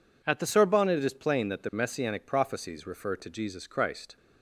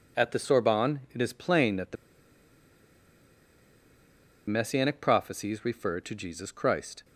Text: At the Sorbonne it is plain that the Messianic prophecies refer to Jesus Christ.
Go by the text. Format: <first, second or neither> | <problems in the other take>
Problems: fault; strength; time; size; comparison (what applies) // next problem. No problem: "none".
first | pauses between "the" and "Messianic"; strong; at 1.9 s; 2.5 s long